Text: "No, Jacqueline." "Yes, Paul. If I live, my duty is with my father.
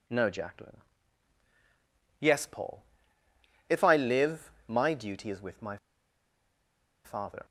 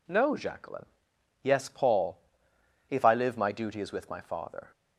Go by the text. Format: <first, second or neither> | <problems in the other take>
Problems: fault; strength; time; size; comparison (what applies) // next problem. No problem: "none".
second | pauses between "my" and "father"; strong; at 5.7 s; 1.2 s long